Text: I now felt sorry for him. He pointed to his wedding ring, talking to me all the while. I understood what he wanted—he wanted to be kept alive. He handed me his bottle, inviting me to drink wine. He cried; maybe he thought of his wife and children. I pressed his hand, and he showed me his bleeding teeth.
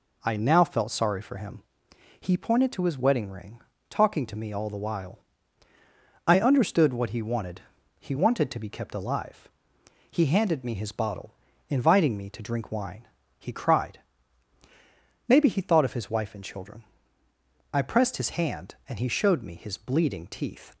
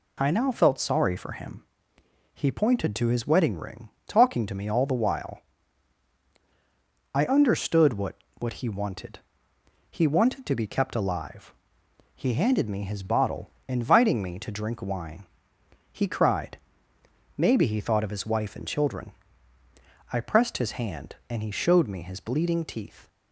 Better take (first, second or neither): first